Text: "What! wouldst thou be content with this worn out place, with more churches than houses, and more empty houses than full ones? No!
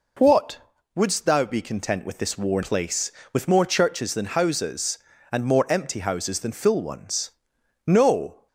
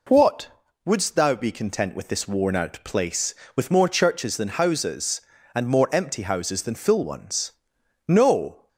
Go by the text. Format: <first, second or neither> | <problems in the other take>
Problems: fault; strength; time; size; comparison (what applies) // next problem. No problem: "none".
second | skips "out"; at 2.6 s